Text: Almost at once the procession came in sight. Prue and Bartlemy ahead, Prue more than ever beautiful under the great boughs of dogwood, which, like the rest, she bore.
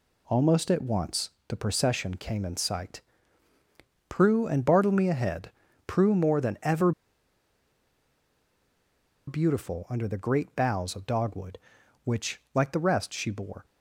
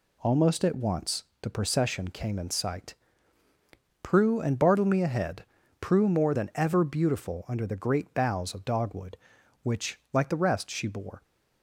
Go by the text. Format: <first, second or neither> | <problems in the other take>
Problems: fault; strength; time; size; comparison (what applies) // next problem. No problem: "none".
second | pauses between "once" and "the"; slight; at 1.3 s; 0.18 s long; slight in the second // pauses between "ever" and "beautiful"; strong; at 6.9 s; 2.3 s long